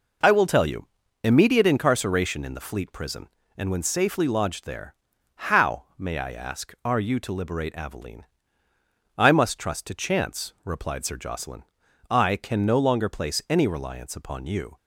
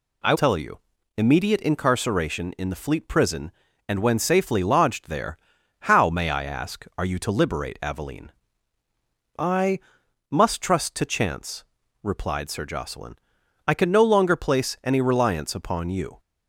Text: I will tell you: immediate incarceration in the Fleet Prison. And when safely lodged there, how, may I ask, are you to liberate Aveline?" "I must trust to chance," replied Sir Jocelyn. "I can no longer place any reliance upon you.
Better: first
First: none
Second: skips "will"; at 0.3 s // pauses between "I" and "must"; noticeable; at 9.7 s; 0.52 s long

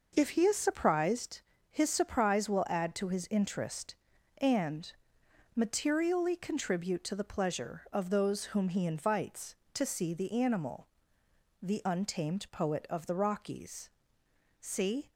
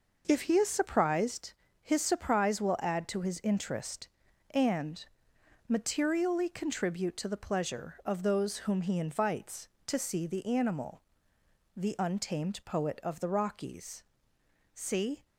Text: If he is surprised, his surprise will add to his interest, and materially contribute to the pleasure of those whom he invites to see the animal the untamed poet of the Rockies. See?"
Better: neither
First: pauses between "and" and "materially"; noticeable; at 4.9 s; 0.64 s long // pauses between "animal" and "the"; noticeable; at 10.8 s; 0.76 s long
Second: pauses between "and" and "materially"; noticeable; at 5.0 s; 0.64 s long // pauses between "animal" and "the"; noticeable; at 11.0 s; 0.76 s long

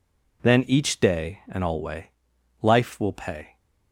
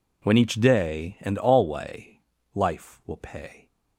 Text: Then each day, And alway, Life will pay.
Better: first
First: none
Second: says "When" for "Then"; at 0.2 s

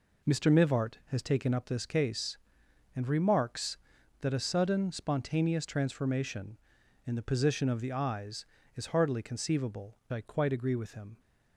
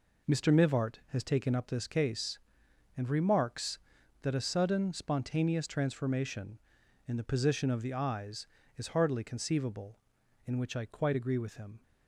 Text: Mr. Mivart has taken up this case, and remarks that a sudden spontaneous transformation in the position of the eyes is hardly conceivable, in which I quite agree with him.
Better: second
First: skips "in which"; at 10.0 s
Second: none

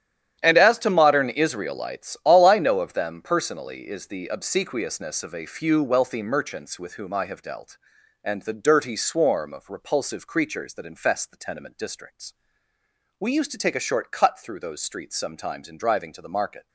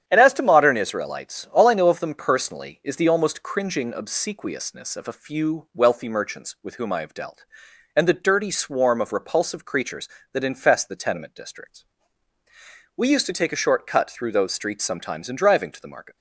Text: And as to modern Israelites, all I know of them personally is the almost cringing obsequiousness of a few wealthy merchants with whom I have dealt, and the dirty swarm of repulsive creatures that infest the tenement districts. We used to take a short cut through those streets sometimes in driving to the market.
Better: second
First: starts louder than the rest; strong; until 1.4 s; 10.5 dB // skips "almost cringing"; at 4.2 s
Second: starts louder than the rest; strong; until 1.1 s; 9.5 dB

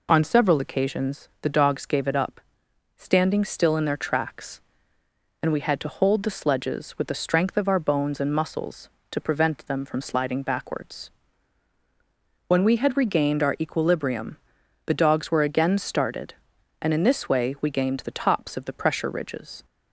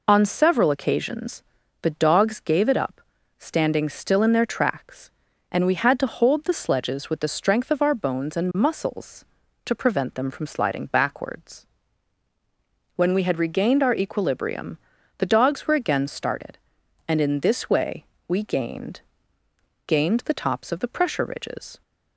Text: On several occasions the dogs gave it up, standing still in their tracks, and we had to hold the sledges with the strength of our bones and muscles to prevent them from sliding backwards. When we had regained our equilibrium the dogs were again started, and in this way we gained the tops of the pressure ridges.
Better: first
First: pauses between "equilibrium" and "the"; noticeable; at 14.3 s; 0.48 s long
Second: pauses between "occasions" and "the"; at 1.4 s; 0.38 s long // pauses between "equilibrium" and "the"; at 14.7 s; 0.40 s long // pauses between "way" and "we"; slight; at 18.0 s; 0.24 s long // says "gained" twice; at 19.8 s

